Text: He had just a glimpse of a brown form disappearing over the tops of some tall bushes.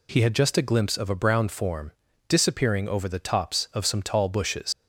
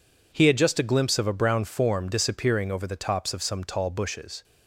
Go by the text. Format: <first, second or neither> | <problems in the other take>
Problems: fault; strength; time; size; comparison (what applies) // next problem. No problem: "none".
second | pauses between "form" and "disappearing"; slight; at 1.9 s; 0.34 s long // leaves "bushes" unfinished; at 4.7 s; 95 ms